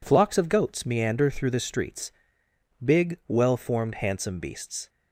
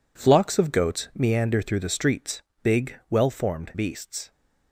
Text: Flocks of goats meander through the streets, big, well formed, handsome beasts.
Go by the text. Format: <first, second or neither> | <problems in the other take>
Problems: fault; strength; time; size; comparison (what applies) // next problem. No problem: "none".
first | skips "handsome"; at 3.7 s